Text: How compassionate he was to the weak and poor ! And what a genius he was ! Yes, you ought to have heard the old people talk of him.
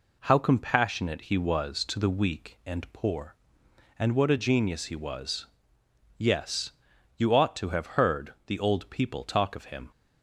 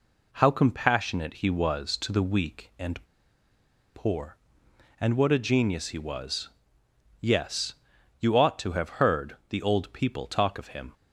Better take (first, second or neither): first